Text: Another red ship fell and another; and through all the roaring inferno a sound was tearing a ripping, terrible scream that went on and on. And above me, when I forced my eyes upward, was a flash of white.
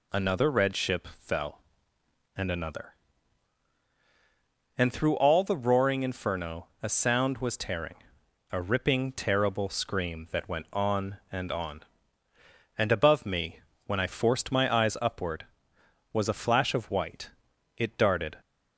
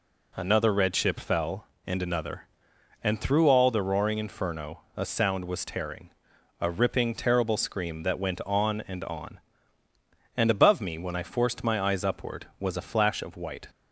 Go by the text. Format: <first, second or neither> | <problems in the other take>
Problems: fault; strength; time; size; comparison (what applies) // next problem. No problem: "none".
second | pauses between "inferno" and "a"; slight; at 6.6 s; 0.16 s long; slight in the second // pauses between "tearing" and "a"; noticeable; at 7.9 s; 0.58 s long; noticeable in the second // goes on to say "It darted"; noticeable; from 17.7 s on; 0.62 s long